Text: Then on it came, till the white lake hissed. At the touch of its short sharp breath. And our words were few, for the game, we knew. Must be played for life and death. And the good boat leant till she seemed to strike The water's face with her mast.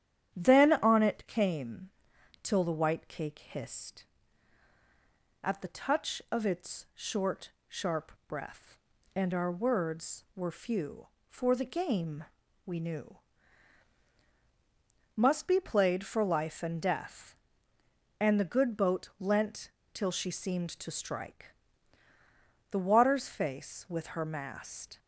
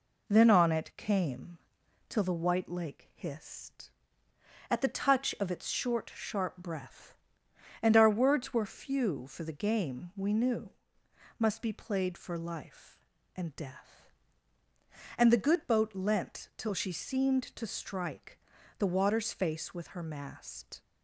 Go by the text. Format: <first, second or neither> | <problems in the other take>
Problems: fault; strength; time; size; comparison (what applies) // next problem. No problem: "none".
second | starts louder than the rest; strong; until 1.3 s; 10 dB // says "cake" for "lake"; at 3.0 s // pauses between "short" and "sharp"; slight; at 7.5 s; 0.18 s long // pauses between "sharp" and "breath"; slight; at 8.1 s; 0.16 s long // pauses between "leant" and "till"; slight; at 19.7 s; 0.22 s long // pauses between "strike" and "The"; at 21.5 s; 1.1 s long; also in the second